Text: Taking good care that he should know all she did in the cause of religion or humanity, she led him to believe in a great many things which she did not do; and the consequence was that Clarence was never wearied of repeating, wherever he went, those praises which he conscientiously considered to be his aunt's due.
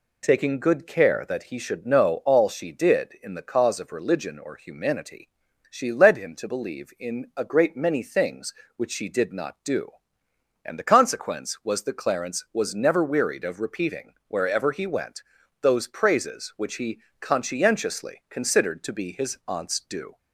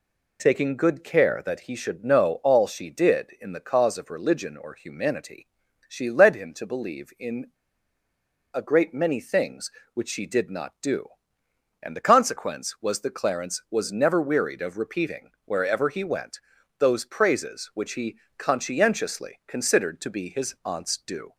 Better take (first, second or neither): first